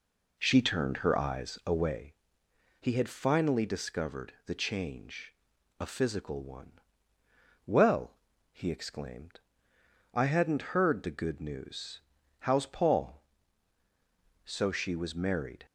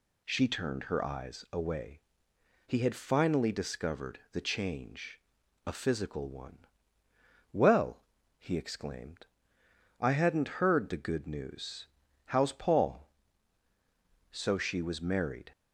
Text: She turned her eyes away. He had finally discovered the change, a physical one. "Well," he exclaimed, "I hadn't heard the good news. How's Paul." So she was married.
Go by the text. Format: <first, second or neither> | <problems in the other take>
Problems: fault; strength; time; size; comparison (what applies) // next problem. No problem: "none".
second | starts louder than the rest; until 2.1 s; 3.5 dB